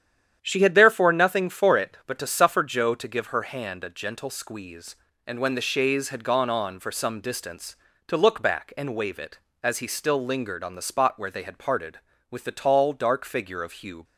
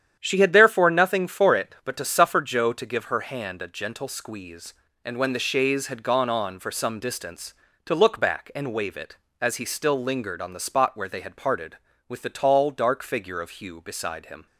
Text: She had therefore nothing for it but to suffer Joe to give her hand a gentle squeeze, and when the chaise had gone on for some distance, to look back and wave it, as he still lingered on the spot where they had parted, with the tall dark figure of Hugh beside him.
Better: second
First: starts louder than the rest; strong; until 1.4 s; 9.5 dB // stops before "beside him"; at 14.0 s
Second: starts louder than the rest; strong; until 1.2 s; 9.5 dB

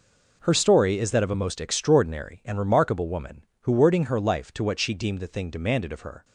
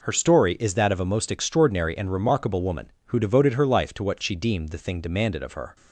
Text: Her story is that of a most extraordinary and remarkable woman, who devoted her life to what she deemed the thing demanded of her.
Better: second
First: says "wording" for "devoted"; at 3.7 s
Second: none

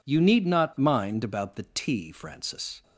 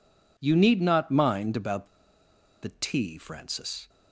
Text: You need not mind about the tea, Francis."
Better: first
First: none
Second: pauses between "about" and "the"; noticeable; at 1.8 s; 0.75 s long

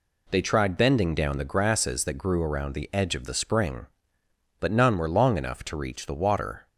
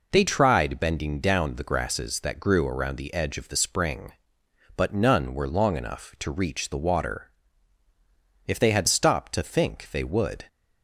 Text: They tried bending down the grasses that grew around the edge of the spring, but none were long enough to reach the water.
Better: first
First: none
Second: goes on to say "If they had stopped to think they would"; strong; from 8.4 s on; 2.0 s long

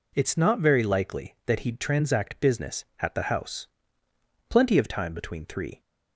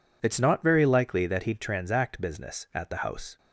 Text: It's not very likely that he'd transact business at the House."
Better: second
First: goes on to say "Plenty of time between three"; noticeable; from 4.5 s on; 1.3 s long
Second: none

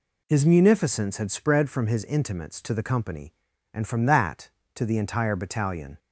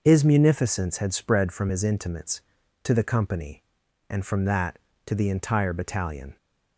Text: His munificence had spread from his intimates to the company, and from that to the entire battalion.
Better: neither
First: none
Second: none

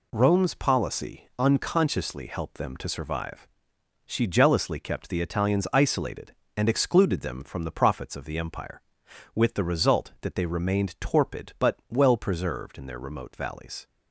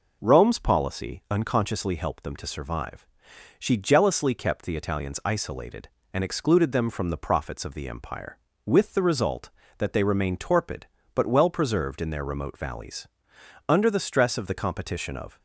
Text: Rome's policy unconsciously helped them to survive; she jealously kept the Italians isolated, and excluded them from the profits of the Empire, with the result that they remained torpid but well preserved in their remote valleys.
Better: first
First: none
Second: goes on to say "Under the stress of the competition of"; strong; from 13.6 s on; 1.7 s long

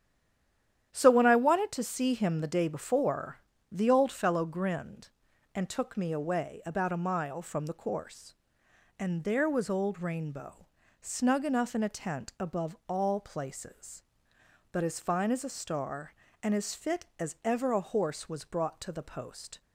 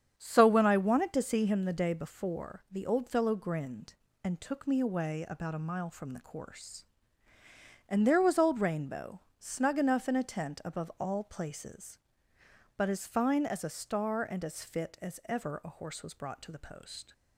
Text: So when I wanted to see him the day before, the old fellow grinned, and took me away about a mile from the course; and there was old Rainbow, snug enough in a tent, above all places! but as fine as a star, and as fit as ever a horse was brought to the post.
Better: second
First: stays silent before the first word; slight; until 0.9 s; 0.9 s long // starts louder than the rest; strong; until 1.9 s; 10.5 dB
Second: starts louder than the rest; strong; until 1.1 s; 8 dB

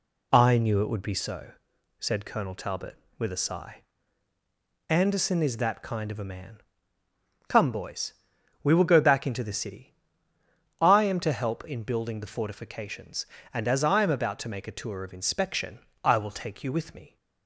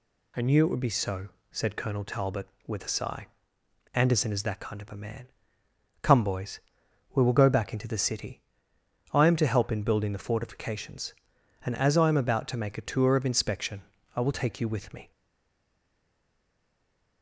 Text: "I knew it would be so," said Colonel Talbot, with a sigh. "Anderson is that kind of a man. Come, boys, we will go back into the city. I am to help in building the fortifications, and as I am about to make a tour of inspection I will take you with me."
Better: first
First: pauses between "inspection" and "I"; slight; at 15.7 s; 0.24 s long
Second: pauses between "inspection" and "I"; slight; at 13.8 s; 0.32 s long // stays silent after the last word; from 15.1 s on; 2.1 s long

